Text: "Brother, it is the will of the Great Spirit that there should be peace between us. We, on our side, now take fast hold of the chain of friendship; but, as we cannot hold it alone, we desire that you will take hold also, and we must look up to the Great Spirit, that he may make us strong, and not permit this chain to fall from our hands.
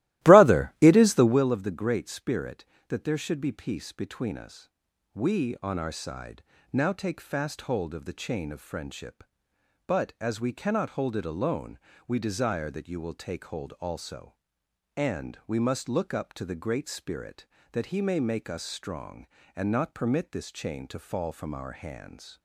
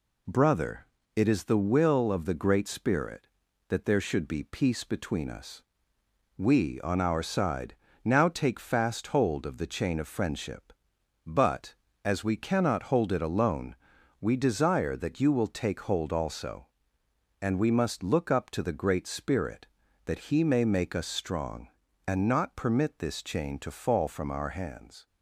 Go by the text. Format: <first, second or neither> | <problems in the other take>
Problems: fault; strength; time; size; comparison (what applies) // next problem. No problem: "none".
second | starts louder than the rest; strong; until 1.5 s; 16.5 dB